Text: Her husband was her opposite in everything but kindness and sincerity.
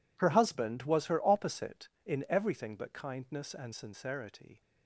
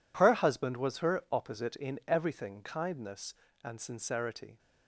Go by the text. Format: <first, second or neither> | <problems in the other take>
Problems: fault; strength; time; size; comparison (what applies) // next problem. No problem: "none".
first | skips "but"; at 2.6 s